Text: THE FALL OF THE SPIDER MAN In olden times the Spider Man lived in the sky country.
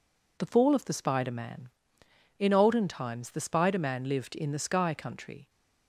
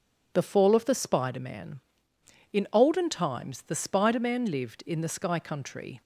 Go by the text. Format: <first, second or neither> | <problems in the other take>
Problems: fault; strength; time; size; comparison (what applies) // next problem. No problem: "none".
neither | none